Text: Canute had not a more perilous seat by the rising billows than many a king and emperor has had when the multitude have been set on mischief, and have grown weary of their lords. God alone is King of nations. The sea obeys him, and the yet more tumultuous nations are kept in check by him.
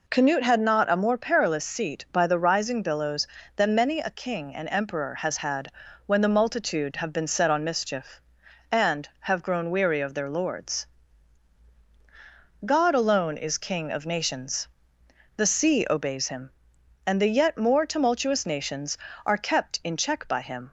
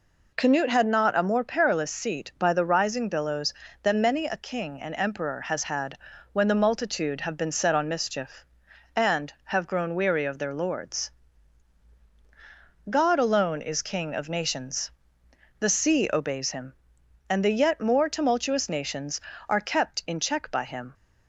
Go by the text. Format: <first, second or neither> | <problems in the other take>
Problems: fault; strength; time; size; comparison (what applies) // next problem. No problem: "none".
neither | pauses between "had" and "when"; the same in both